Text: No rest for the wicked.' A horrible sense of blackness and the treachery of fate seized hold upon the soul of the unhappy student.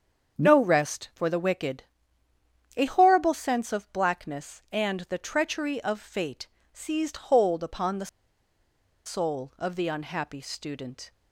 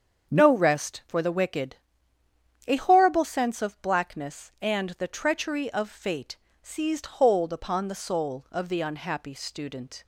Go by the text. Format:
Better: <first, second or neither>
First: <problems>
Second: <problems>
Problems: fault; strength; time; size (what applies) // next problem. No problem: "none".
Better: second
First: starts louder than the rest; until 1.4 s; 7 dB // pauses between "fate" and "seized"; slight; at 6.4 s; 0.24 s long // pauses between "the" and "soul"; at 8.0 s; 0.98 s long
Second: starts louder than the rest; until 1.3 s; 7 dB // pauses between "fate" and "seized"; slight; at 6.3 s; 0.24 s long